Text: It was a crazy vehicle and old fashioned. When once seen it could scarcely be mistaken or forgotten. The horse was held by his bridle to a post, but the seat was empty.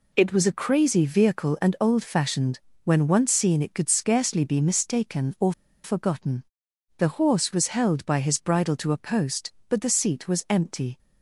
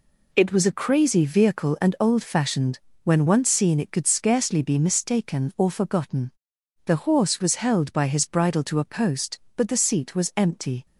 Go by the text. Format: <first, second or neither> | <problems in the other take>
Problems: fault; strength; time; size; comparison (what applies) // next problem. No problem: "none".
second | pauses between "or" and "forgotten"; slight; at 5.5 s; 0.31 s long